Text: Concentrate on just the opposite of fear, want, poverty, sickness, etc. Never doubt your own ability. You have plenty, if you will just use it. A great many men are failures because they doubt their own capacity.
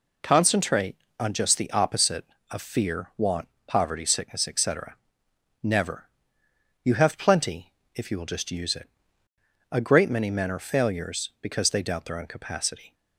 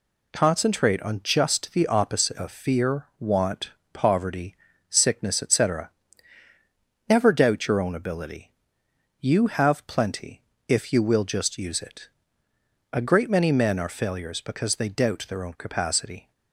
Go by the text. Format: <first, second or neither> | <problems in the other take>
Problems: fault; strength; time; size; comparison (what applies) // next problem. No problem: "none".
second | skips "doubt your own ability"; at 6.4 s